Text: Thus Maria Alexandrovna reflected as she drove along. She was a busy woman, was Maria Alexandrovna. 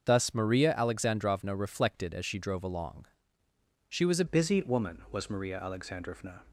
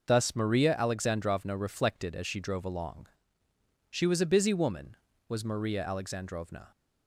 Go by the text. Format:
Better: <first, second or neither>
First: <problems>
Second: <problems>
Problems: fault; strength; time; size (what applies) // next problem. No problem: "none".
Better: second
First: starts louder than the rest; until 1.1 s; 6.5 dB // changes voice at "busy"; from 4.2 s on; 2.2 s long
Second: none